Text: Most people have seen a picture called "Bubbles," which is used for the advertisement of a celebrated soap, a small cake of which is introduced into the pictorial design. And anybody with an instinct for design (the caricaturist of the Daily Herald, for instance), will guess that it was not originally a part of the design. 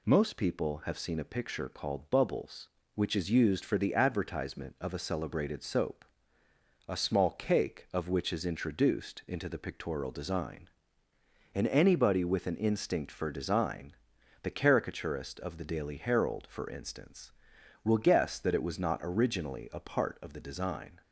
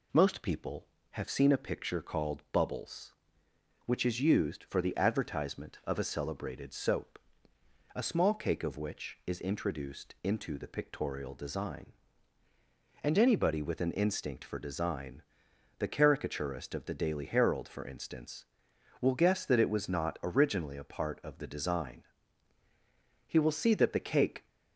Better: first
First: none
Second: goes on to say "He will see that the cake"; noticeable; from 23.2 s on; 1.2 s long

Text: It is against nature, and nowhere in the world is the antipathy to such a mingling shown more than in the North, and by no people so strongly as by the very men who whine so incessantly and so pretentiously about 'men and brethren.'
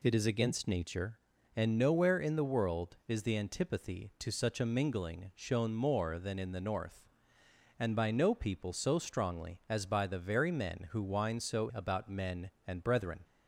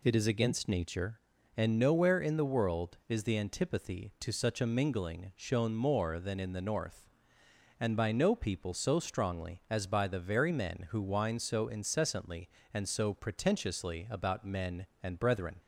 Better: second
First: skips "incessantly and so pretentiously"; at 11.7 s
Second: none

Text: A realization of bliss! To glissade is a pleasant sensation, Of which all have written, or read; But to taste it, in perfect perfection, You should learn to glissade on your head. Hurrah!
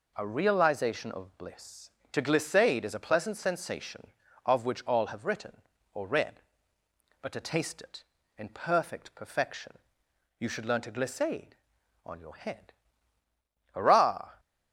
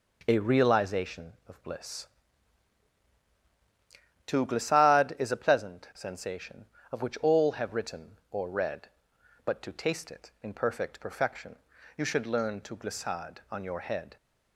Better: first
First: none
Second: stops before "Hurrah"; at 14.1 s

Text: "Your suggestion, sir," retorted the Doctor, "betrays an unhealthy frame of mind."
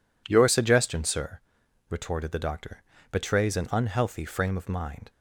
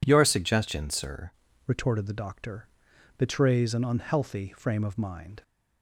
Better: first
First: none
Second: changes voice at "retorted"; from 1.6 s on; 3.8 s long

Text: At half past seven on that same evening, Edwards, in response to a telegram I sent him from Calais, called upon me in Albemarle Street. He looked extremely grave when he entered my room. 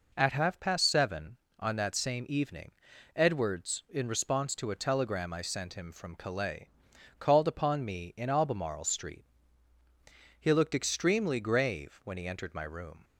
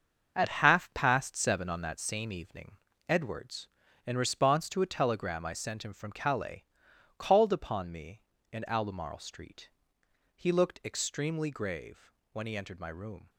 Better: first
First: none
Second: gets quieter; strong; throughout; 10 dB // pauses between "grave" and "when"; slight; at 12.1 s; 0.20 s long

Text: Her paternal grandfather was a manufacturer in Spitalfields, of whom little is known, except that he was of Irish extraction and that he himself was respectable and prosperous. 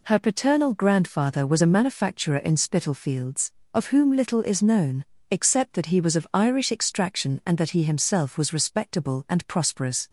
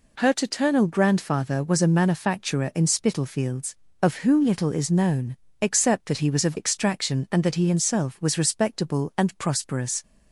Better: first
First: none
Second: skips "Irish"; at 6.5 s

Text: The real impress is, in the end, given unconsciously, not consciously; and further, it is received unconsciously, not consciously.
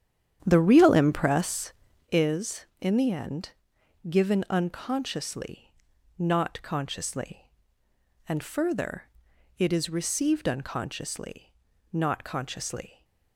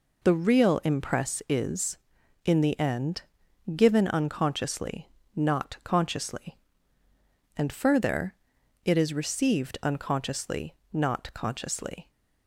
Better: second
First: starts louder than the rest; strong; until 2.3 s; 9.5 dB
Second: none

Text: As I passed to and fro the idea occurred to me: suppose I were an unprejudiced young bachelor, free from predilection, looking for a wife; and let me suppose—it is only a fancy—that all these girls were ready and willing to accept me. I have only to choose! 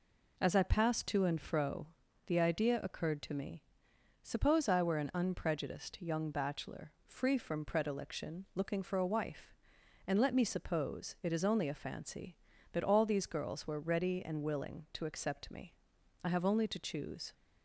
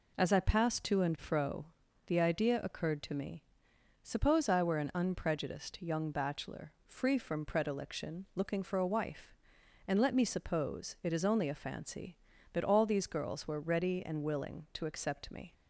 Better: first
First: pauses between "fro" and "the"; at 1.8 s; 0.40 s long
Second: pauses between "fro" and "the"; at 1.6 s; 0.42 s long // stops before "I have only to choose"; at 15.5 s

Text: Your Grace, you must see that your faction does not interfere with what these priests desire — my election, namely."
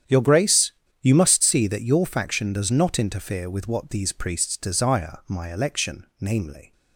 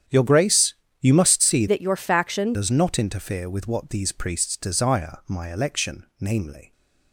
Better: first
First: starts louder than the rest; strong; until 1.3 s; 9.5 dB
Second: starts louder than the rest; strong; until 1.3 s; 9.5 dB // changes voice from "that" to "faction"; from 1.6 to 2.5 s; 0.9 s long

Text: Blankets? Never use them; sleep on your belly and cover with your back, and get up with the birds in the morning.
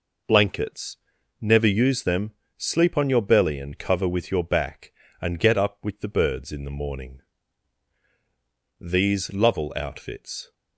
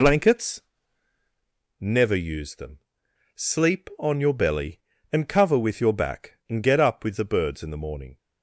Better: second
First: goes on to say "These Lovell outfits"; strong; from 8.7 s on; 1.7 s long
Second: none

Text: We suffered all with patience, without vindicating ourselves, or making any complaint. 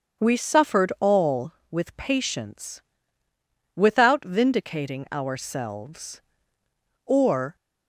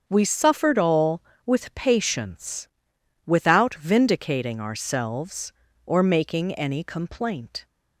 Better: second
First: starts louder than the rest; strong; until 1.2 s; 7 dB // stops before "making any complaint"; at 7.5 s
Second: starts louder than the rest; until 1.0 s; 7 dB

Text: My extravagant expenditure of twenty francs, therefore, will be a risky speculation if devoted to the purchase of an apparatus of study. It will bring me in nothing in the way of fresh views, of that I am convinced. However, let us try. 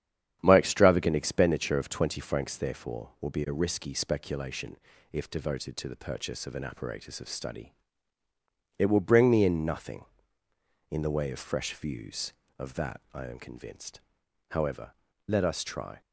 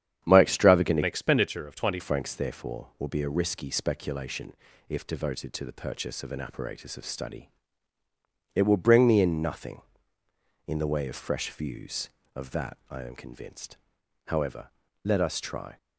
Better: first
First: starts louder than the rest; strong; until 1.4 s; 9 dB // pauses between "speculation" and "if"; slight; at 4.7 s; 0.36 s long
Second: starts louder than the rest; strong; until 1.3 s; 9 dB // changes voice from "expenditure" to "twenty"; from 1.0 to 2.0 s; 1.0 s long // pauses between "speculation" and "if"; slight; at 4.5 s; 0.36 s long

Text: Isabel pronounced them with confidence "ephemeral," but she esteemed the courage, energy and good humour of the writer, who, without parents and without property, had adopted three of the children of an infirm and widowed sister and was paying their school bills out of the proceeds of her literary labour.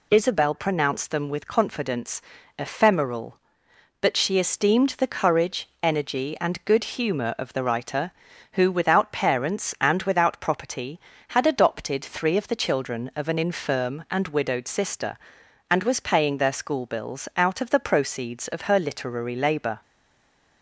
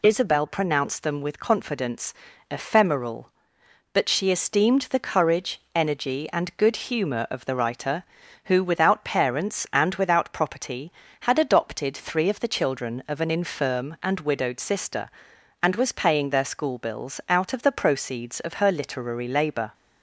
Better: second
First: pauses between "confidence" and "ephemeral"; at 2.1 s; 0.38 s long // stays silent after the last word; slight; from 19.8 s on; 0.8 s long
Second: pauses between "confidence" and "ephemeral"; at 2.1 s; 0.38 s long

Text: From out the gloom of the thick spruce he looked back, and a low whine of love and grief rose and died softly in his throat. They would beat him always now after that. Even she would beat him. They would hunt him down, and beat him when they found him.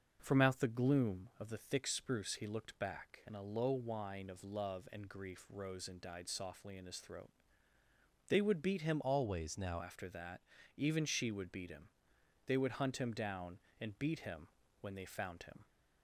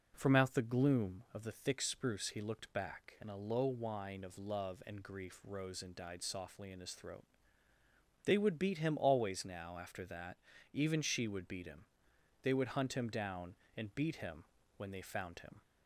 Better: second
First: starts louder than the rest; noticeable; until 1.2 s; 6 dB // changes voice from "always" to "now"; from 9.0 to 9.8 s; 0.8 s long // pauses between "him" and "when"; slight; at 14.4 s; 0.32 s long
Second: pauses between "him" and "when"; slight; at 14.4 s; 0.32 s long

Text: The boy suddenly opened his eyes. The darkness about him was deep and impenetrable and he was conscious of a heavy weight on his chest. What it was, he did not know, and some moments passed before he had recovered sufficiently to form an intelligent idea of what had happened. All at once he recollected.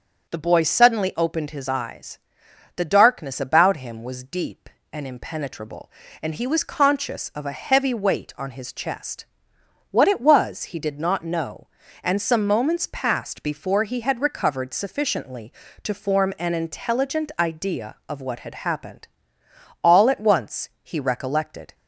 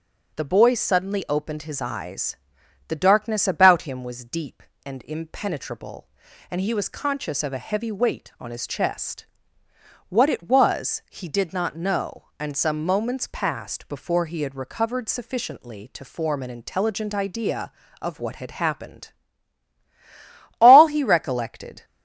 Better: first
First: none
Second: starts louder than the rest; noticeable; until 1.3 s; 6 dB // skips "at once"; at 20.8 s

